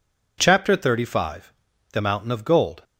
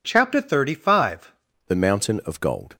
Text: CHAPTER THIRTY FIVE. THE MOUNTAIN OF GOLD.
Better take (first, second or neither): first